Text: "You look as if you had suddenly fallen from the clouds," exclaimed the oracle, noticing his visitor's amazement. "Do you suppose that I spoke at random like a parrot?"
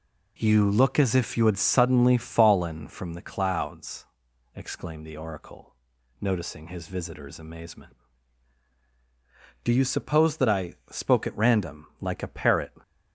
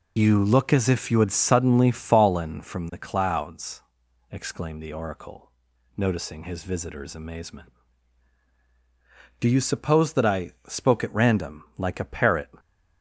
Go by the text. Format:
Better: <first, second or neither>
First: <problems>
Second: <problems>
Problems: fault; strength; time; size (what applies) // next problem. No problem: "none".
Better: first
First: pauses between "I" and "spoke"; slight; at 10.7 s; 0.18 s long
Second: loses the start of "You"; at 0.1 s; 45 ms // pauses between "I" and "spoke"; slight; at 10.5 s; 0.18 s long